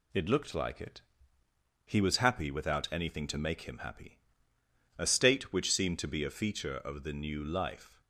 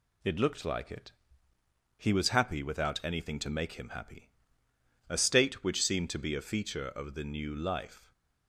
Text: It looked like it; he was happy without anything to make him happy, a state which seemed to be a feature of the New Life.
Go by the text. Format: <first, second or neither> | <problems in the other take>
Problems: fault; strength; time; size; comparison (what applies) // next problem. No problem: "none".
neither | none